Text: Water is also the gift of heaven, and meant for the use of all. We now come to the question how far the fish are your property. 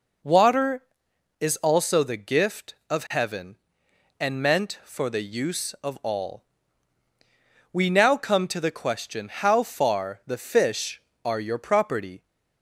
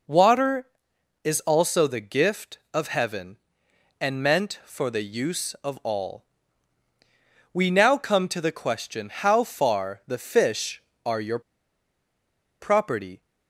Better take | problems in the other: first | pauses between "your" and "property"; at 11.3 s; 1.2 s long

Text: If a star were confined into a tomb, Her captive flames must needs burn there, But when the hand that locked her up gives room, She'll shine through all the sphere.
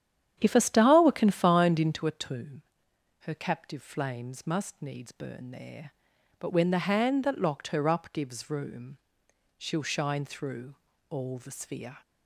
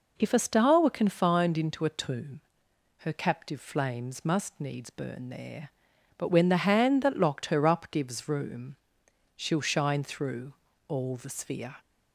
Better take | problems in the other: second | starts louder than the rest; strong; until 2.2 s; 10 dB // pauses between "through" and "all"; slight; at 10.7 s; 0.34 s long; slight in the second

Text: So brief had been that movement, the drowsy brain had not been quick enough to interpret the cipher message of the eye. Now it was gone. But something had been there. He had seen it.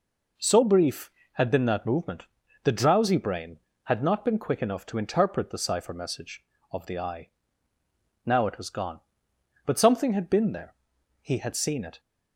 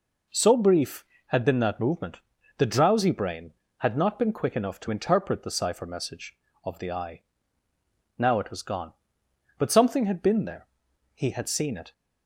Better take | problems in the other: neither | none

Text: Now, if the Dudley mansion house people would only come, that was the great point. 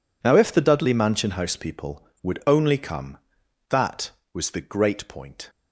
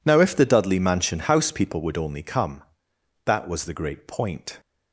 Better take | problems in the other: neither | none

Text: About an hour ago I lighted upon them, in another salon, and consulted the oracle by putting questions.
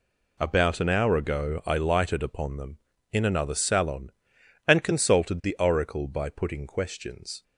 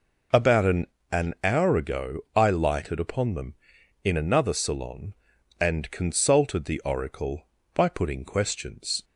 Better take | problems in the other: first | says "an" twice; at 1.0 s // pauses between "ago" and "I"; slight; at 2.1 s; 0.16 s long

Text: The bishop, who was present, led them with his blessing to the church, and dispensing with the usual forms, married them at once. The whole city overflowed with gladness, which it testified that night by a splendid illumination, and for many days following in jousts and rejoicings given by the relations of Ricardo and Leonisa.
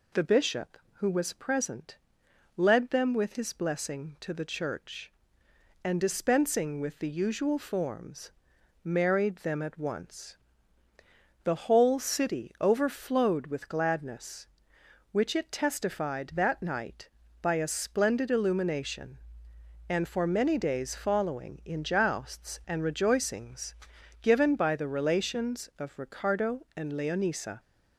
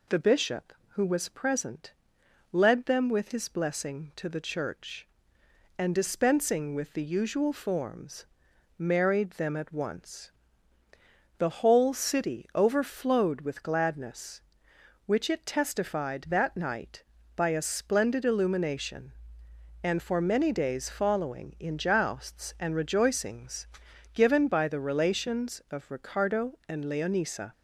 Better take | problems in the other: neither | pauses between "rejoicings" and "given"; noticeable; the same in both

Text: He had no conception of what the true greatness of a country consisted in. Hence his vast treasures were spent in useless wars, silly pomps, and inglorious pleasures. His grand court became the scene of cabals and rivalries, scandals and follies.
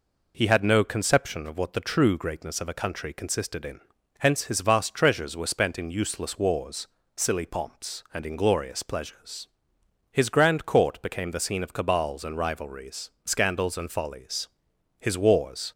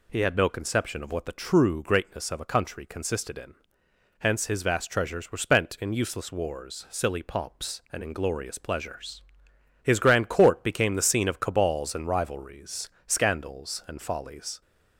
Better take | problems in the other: second | goes on to say "His wars"; noticeable; from 14.9 s on; 0.72 s long

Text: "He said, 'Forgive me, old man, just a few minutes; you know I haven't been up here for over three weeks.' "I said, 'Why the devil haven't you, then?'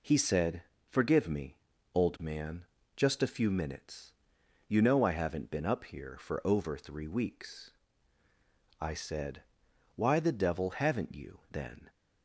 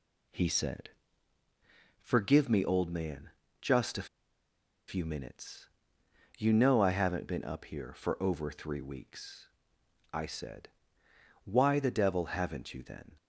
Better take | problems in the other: first | pauses between "a" and "few"; noticeable; at 4.0 s; 0.82 s long

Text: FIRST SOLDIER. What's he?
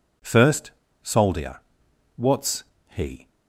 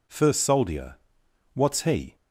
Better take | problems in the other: second | pauses between "FIRST" and "SOLDIER"; slight; at 0.6 s; 0.33 s long // pauses between "What's" and "he"; slight; at 2.6 s; 0.24 s long

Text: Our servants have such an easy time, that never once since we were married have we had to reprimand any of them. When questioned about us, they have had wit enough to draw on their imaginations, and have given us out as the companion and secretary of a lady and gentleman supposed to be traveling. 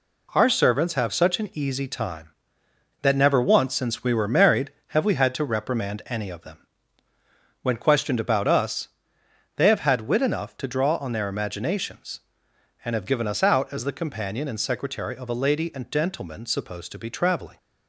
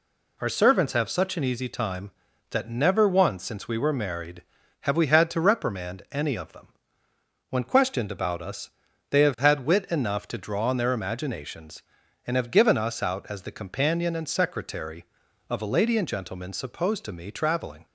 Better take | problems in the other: first | says "me" for "be"; at 17.1 s

